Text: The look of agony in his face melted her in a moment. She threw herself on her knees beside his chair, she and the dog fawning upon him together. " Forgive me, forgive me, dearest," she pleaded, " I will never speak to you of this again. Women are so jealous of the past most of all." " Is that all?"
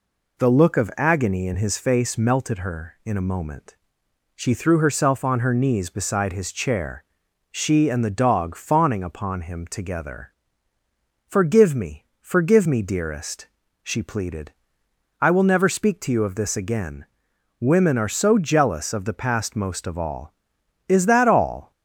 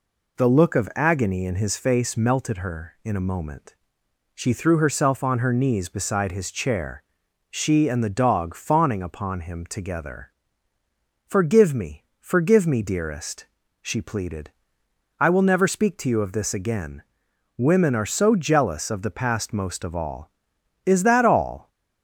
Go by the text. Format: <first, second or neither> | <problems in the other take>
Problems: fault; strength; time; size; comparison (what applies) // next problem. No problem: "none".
neither | none